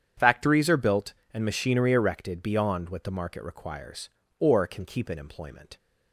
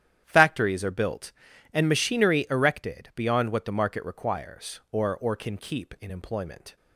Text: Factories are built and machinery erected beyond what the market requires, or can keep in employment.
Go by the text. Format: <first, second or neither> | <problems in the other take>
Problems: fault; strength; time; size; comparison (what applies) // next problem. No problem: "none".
first | starts louder than the rest; strong; until 1.2 s; 10 dB; strong in the first // says "or" twice; at 5.1 s